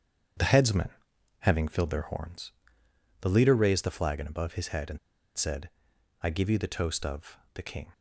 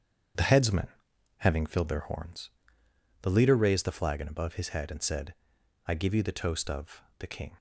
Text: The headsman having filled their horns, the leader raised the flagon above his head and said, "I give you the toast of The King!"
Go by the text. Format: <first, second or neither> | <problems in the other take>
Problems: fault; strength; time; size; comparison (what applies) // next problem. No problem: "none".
second | starts louder than the rest; strong; until 1.8 s; 8 dB; strong in the second // pauses between "headsman" and "having"; noticeable; at 0.8 s; 0.50 s long; noticeable in the second // pauses between "and" and "said"; at 4.9 s; 0.39 s long // pauses between "of" and "The"; slight; at 7.3 s; 0.18 s long; slight in the second